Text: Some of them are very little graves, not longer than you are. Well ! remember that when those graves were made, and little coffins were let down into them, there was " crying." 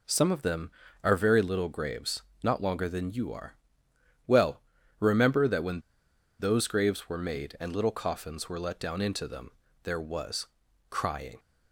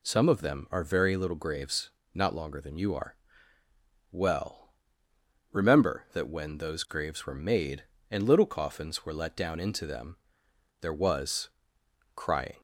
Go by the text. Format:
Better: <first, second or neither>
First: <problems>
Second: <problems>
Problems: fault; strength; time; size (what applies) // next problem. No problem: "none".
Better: second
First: pauses between "when" and "those"; noticeable; at 5.8 s; 0.57 s long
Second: none